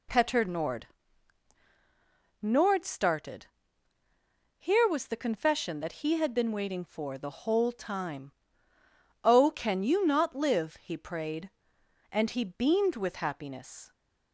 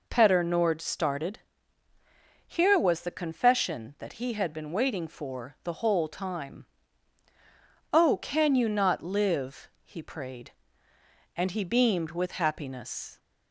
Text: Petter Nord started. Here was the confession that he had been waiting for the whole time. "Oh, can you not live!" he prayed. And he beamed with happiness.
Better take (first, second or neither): second